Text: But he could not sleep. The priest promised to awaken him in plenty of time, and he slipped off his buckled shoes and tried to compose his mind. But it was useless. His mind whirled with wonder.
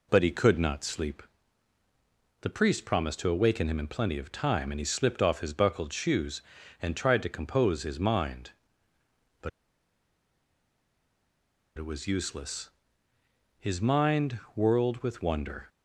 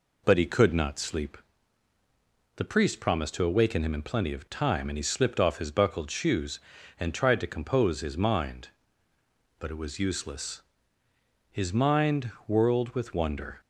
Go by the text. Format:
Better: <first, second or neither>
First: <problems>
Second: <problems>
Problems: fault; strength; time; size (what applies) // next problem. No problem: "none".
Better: second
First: pauses between "But" and "it"; strong; at 9.4 s; 2.2 s long // pauses between "mind" and "whirled"; slight; at 14.3 s; 0.18 s long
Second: pauses between "mind" and "whirled"; slight; at 12.3 s; 0.18 s long